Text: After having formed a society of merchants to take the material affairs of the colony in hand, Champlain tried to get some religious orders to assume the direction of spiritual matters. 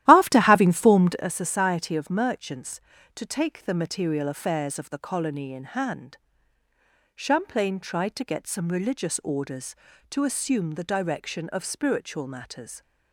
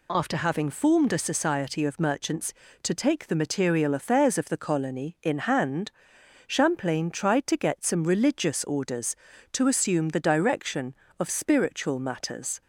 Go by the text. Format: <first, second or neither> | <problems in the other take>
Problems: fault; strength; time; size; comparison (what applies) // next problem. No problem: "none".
second | starts louder than the rest; strong; until 1.3 s; 13.5 dB